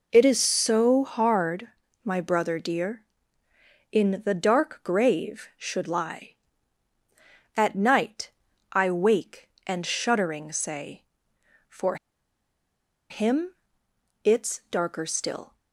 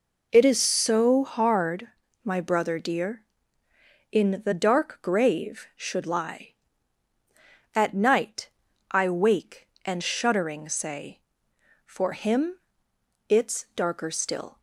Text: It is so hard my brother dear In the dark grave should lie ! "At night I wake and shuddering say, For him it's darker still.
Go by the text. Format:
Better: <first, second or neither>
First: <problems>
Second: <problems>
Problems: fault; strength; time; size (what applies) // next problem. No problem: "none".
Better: second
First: pauses between "hard" and "my"; slight; at 1.6 s; 0.36 s long // pauses between "night" and "I"; at 8.3 s; 0.40 s long // pauses between "For" and "him"; at 11.9 s; 1.1 s long // pauses between "him" and "it's"; noticeable; at 13.5 s; 0.70 s long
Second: pauses between "hard" and "my"; slight; at 1.8 s; 0.36 s long // pauses between "night" and "I"; at 8.4 s; 0.40 s long // pauses between "him" and "it's"; noticeable; at 12.5 s; 0.70 s long